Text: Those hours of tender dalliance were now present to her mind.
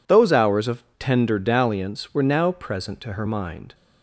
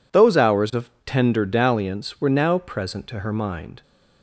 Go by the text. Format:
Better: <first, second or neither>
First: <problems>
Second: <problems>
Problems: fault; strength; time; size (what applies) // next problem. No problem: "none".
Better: neither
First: pauses between "of" and "tender"; slight; at 0.8 s; 0.16 s long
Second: pauses between "of" and "tender"; slight; at 0.8 s; 0.16 s long